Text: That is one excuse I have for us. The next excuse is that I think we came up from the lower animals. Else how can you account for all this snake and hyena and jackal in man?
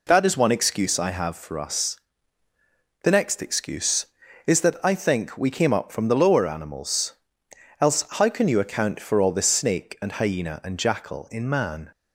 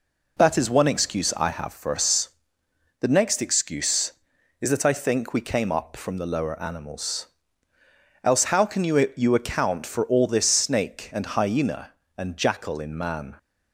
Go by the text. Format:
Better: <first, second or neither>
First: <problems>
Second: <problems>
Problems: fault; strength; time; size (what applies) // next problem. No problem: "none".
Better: first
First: none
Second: says "you" twice; at 9.1 s